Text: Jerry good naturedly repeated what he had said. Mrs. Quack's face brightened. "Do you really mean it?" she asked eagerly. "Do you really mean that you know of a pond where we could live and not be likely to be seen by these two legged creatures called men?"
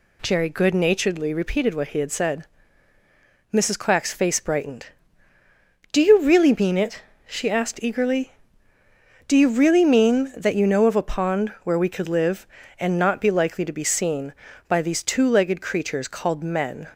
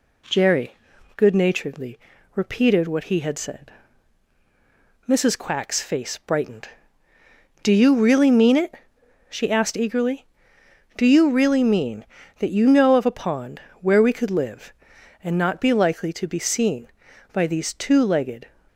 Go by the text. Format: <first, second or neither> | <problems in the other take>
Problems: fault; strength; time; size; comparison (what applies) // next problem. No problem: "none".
first | pauses between "Jerry" and "good"; at 0.7 s; 0.42 s long // pauses between "naturedly" and "repeated"; slight; at 1.9 s; 0.36 s long // pauses between "pond" and "where"; slight; at 13.6 s; 0.22 s long // stops before "creatures called men"; at 18.6 s